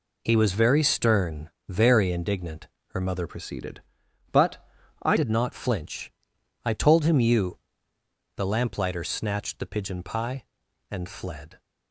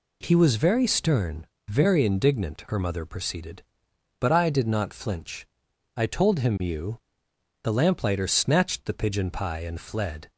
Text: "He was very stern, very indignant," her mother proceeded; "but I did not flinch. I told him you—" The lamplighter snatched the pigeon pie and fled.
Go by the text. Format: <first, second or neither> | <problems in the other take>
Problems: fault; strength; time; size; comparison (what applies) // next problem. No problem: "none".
second | changes voice from "proceeded" to "I"; from 3.2 to 5.1 s; 1.9 s long // pauses between "but" and "I"; at 4.5 s; 0.42 s long